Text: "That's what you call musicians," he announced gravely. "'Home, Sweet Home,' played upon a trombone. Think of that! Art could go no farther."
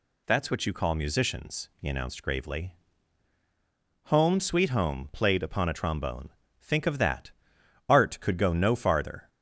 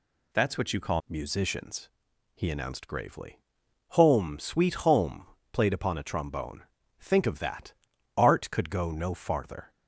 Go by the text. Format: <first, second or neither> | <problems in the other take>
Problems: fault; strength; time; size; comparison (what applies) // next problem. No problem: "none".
first | changes voice at "musicians"; from 1.0 s on; 8.7 s long